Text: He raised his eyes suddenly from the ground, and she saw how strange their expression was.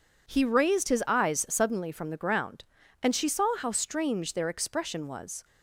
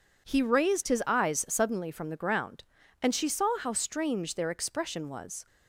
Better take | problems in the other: neither | none

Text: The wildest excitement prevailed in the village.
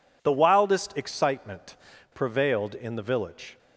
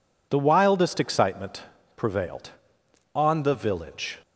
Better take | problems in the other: first | pauses between "excitement" and "prevailed"; slight; at 1.6 s; 0.34 s long; also in the first // says "on" for "in"; at 3.1 s

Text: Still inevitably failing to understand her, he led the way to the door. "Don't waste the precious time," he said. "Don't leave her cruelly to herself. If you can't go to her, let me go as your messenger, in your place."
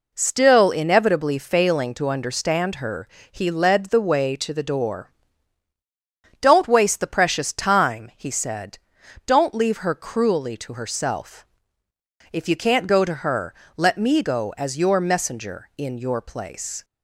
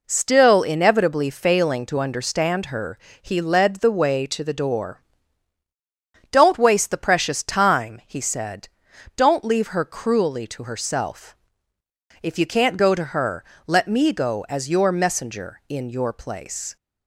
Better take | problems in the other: neither | none

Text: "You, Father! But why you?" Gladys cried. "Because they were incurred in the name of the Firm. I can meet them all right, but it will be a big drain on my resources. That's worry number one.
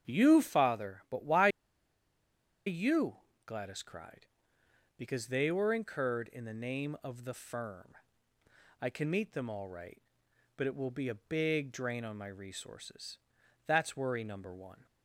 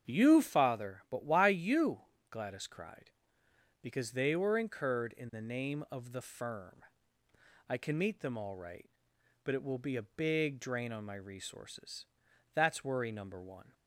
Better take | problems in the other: second | starts louder than the rest; strong; until 1.1 s; 8 dB; strong in the second // pauses between "why" and "you"; at 1.4 s; 1.1 s long

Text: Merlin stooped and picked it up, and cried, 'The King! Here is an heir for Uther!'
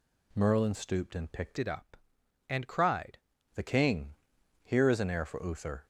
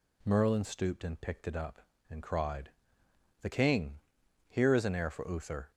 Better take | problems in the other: second | changes voice from "it" to "cried"; from 1.5 to 3.1 s; 1.6 s long

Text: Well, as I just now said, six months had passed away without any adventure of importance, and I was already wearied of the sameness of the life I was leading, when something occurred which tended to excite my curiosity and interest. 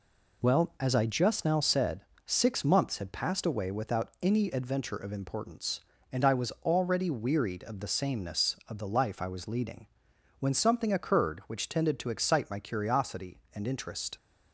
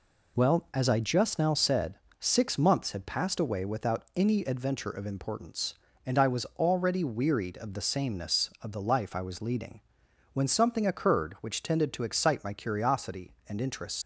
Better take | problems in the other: first | leaves "interest" unfinished; at 14.0 s; 75 ms

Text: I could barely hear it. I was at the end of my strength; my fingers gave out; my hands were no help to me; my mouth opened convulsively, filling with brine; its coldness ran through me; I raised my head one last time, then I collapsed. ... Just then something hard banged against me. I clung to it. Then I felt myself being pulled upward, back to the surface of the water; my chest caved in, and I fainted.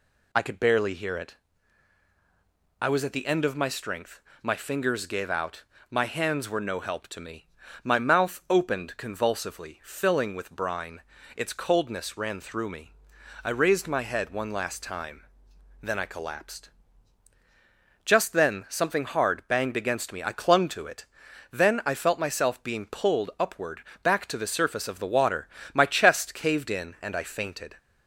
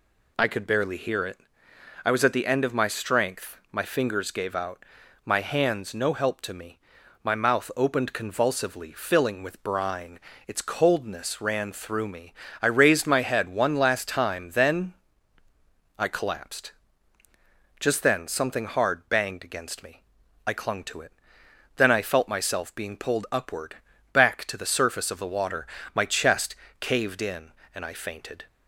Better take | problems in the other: first | skips "were"; at 5.9 s // pauses between "then" and "I"; at 14.9 s; 1.0 s long // pauses between "chest" and "caved"; slight; at 26.5 s; 0.24 s long

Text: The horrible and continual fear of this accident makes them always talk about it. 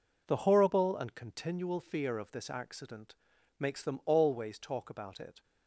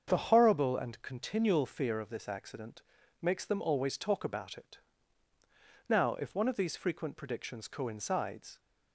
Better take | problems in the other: first | starts louder than the rest; until 1.1 s; 7 dB // pauses between "accident" and "makes"; at 2.8 s; 0.40 s long; also in the first // goes on to say "Now if one of these frequent predictions coincides"; strong; from 5.8 s on; 2.7 s long

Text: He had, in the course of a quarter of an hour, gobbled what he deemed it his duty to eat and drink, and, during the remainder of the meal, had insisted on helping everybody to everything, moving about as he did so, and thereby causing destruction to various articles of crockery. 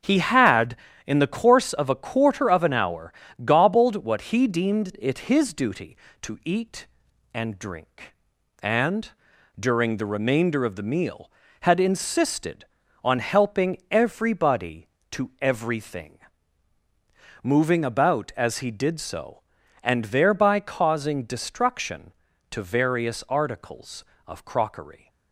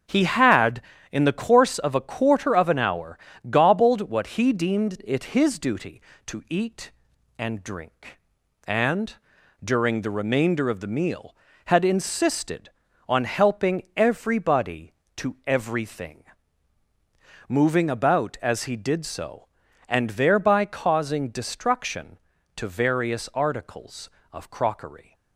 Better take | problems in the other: neither | starts louder than the rest; strong; the same in both

